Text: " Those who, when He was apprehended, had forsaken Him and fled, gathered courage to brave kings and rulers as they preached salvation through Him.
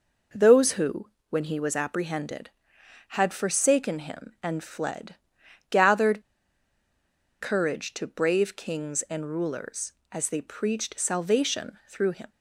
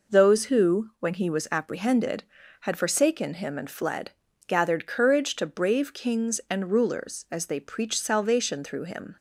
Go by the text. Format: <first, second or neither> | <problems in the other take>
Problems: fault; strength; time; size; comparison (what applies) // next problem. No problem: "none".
second | pauses between "gathered" and "courage"; at 6.2 s; 1.1 s long